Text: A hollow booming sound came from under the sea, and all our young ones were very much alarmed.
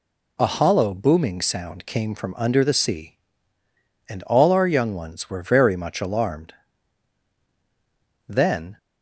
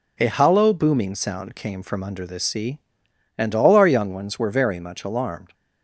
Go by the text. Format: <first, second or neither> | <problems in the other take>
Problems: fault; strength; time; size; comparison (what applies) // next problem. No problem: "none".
second | goes on to say "Then"; slight; from 8.2 s on; 0.48 s long